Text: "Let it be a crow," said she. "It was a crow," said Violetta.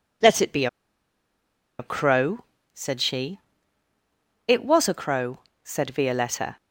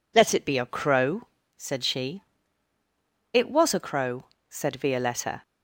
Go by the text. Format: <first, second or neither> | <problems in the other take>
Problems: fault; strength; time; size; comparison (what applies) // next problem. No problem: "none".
second | pauses between "be" and "a"; at 0.6 s; 1.1 s long